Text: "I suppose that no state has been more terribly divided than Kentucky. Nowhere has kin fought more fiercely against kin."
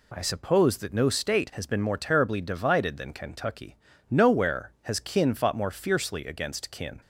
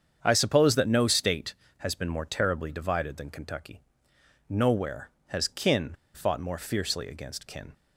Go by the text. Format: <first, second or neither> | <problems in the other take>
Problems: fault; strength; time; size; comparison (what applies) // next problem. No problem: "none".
first | starts louder than the rest; strong; until 1.2 s; 7.5 dB // pauses between "kin" and "fought"; slight; at 5.9 s; 0.21 s long